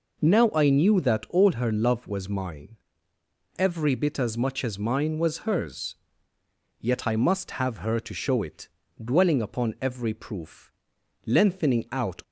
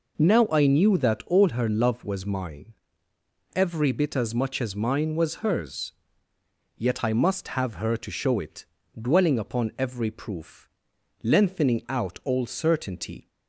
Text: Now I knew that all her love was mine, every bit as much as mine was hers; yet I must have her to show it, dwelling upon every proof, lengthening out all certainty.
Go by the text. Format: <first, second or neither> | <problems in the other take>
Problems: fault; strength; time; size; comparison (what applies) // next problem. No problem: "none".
second | stops before "all certainty"; at 12.2 s